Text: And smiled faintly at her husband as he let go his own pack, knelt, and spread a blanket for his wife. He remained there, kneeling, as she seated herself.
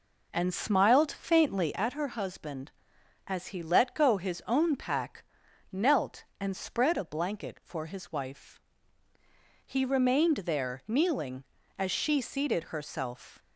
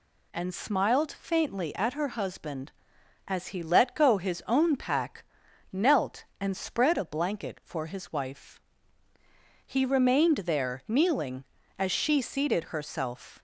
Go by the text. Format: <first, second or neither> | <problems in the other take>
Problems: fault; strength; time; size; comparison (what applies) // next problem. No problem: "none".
second | starts louder than the rest; noticeable; until 1.8 s; 4 dB